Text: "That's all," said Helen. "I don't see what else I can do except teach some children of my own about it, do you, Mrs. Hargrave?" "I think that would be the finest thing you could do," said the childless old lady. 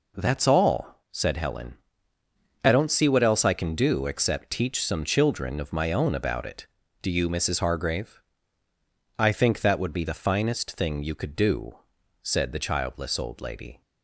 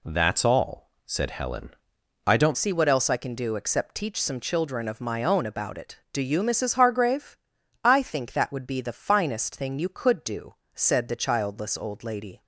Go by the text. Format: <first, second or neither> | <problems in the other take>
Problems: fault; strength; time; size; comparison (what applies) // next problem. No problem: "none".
first | changes voice at "see"; from 2.5 s on; 9.9 s long